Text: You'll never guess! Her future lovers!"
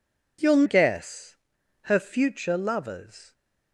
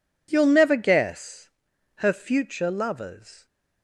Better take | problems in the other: second | skips "never"; at 0.6 s

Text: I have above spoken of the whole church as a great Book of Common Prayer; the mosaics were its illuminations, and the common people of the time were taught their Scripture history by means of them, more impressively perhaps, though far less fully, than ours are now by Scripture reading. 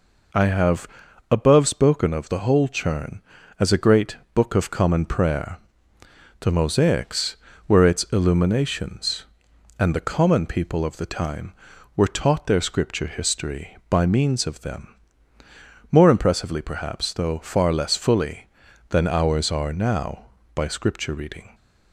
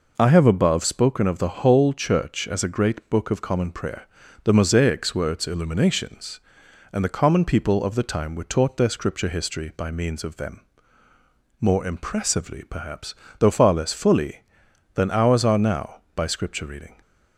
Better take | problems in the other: second | pauses between "have" and "above"; at 0.8 s; 0.44 s long // says "churn" for "church"; at 2.6 s // pauses between "great" and "Book"; slight; at 4.1 s; 0.20 s long

